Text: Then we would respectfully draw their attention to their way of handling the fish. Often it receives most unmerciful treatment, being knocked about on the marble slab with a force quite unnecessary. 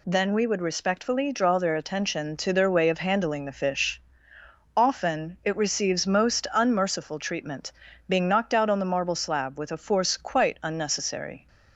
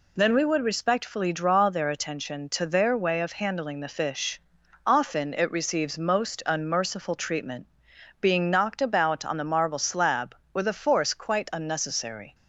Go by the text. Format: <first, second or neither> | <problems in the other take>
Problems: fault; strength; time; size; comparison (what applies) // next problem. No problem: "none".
second | says "out" for "about"; at 8.5 s